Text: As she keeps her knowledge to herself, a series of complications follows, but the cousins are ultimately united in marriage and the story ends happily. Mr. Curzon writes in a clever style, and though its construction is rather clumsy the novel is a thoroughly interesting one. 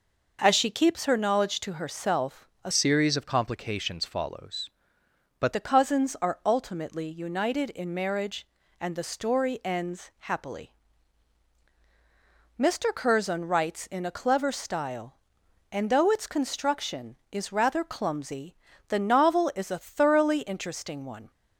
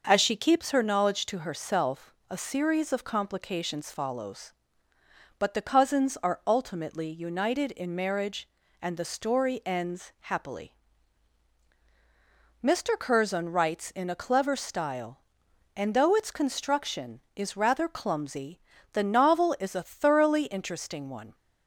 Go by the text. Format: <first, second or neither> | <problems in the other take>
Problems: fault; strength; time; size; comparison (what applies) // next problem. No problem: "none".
second | changes voice from "series" to "but"; from 2.7 to 5.5 s; 2.8 s long // pauses between "clumsy" and "the"; slight; at 18.5 s; 0.32 s long; slight in the second